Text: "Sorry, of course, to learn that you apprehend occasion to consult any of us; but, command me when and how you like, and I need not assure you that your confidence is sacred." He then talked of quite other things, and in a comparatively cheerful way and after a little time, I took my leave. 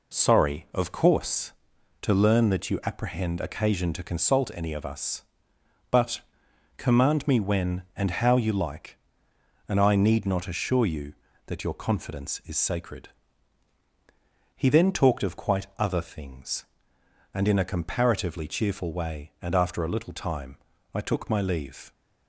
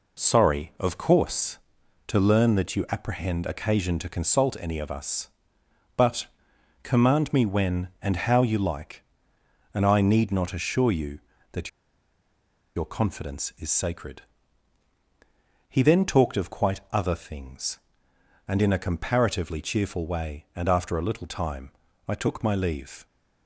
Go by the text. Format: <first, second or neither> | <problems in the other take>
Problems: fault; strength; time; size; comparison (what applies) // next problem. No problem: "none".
first | pauses between "that" and "your"; at 11.6 s; 1.0 s long